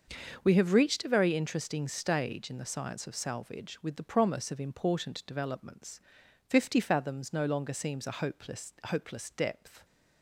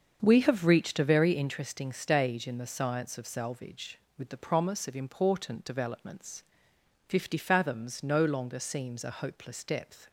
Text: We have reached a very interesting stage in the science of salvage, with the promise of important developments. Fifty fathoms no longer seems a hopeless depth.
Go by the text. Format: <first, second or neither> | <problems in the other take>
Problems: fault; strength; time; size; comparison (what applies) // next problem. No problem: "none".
second | starts louder than the rest; until 1.4 s; 6 dB; also in the second // says "hopeless" twice; at 8.8 s